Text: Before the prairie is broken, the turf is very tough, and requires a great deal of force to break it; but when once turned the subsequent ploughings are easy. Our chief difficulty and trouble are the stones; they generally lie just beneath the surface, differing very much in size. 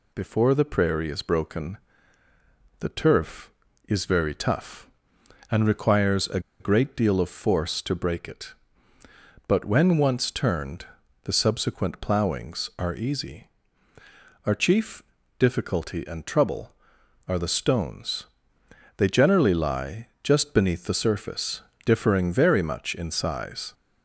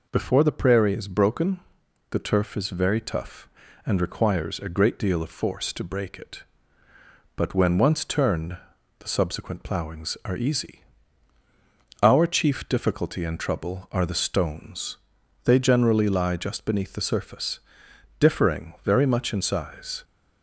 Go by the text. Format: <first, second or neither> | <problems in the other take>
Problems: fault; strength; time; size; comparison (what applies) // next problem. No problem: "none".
second | pauses between "a" and "great"; slight; at 6.3 s; 0.20 s long // pauses between "turned" and "the"; at 10.8 s; 0.38 s long; also in the second // pauses between "chief" and "difficulty"; at 15.0 s; 0.38 s long